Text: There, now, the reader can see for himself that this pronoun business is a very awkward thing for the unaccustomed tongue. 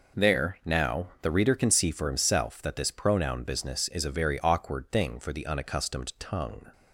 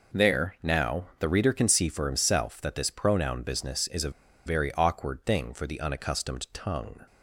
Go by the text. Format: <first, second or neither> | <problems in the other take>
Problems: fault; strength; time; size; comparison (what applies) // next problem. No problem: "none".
first | pauses between "a" and "very"; slight; at 4.1 s; 0.35 s long